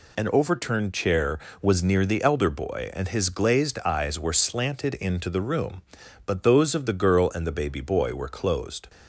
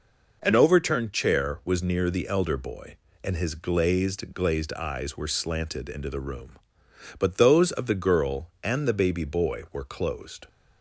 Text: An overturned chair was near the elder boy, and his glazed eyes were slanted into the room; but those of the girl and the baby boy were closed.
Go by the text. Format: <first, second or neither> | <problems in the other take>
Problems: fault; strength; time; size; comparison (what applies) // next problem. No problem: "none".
first | says "glazed" twice; at 4.3 s